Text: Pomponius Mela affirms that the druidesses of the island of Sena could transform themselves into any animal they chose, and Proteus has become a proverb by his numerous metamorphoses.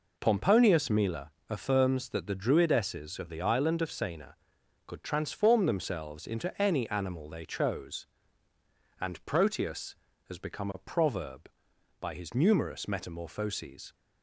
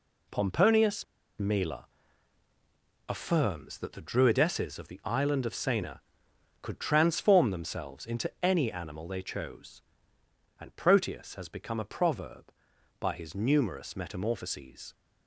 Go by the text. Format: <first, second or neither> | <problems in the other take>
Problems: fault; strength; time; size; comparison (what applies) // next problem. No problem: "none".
first | pauses between "Pomponius" and "Mela"; slight; at 1.0 s; 0.34 s long // pauses between "Mela" and "affirms"; at 1.8 s; 1.2 s long; slight in the first